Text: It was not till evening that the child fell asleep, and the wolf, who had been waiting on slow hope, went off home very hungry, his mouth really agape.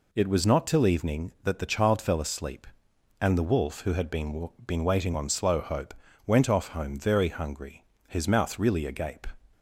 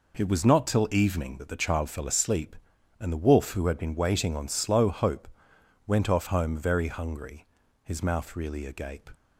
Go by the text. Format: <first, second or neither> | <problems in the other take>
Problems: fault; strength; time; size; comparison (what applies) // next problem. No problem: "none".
second | says "been" twice; at 4.6 s